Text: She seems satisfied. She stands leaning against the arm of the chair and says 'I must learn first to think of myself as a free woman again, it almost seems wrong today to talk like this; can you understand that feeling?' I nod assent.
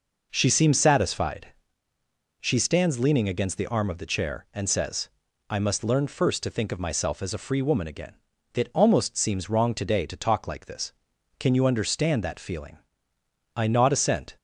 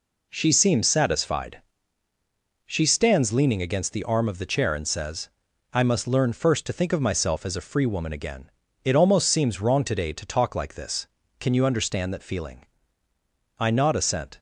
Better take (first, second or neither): neither